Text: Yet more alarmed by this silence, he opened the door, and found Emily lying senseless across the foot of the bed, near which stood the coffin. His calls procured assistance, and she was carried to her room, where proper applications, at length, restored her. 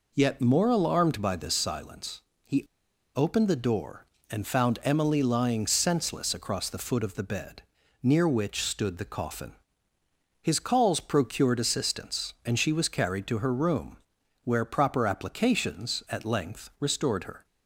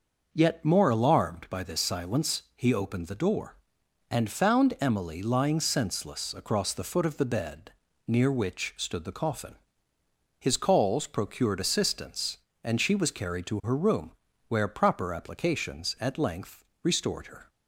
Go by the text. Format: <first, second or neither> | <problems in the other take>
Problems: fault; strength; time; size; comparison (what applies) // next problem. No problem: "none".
second | pauses between "he" and "opened"; noticeable; at 2.6 s; 0.52 s long